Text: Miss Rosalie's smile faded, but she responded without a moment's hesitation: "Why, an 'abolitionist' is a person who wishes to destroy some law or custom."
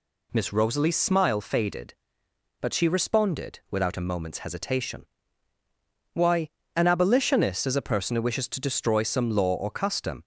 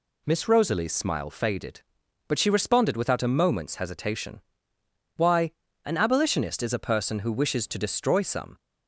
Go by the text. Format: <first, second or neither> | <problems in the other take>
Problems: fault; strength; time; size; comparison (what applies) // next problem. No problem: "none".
first | stops before "law or custom"; at 8.5 s